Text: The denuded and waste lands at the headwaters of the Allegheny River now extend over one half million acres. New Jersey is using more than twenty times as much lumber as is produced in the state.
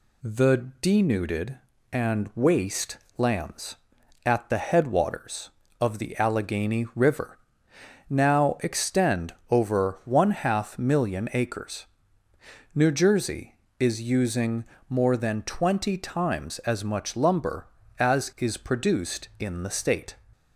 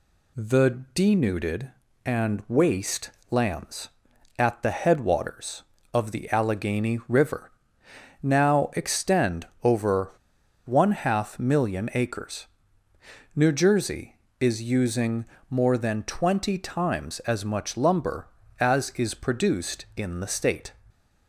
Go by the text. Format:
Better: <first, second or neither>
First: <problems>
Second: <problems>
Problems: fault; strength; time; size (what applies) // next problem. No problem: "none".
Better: first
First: pauses between "waste" and "lands"; slight; at 2.9 s; 0.20 s long // pauses between "River" and "now"; noticeable; at 7.3 s; 0.68 s long // pauses between "extend" and "over"; slight; at 9.3 s; 0.16 s long // pauses between "using" and "more"; slight; at 14.6 s; 0.26 s long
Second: pauses between "waste" and "lands"; slight; at 3.0 s; 0.20 s long // pauses between "River" and "now"; noticeable; at 7.5 s; 0.68 s long // pauses between "extend" and "over"; slight; at 9.4 s; 0.16 s long // pauses between "over" and "one"; noticeable; at 10.0 s; 0.56 s long // pauses between "using" and "more"; slight; at 15.2 s; 0.26 s long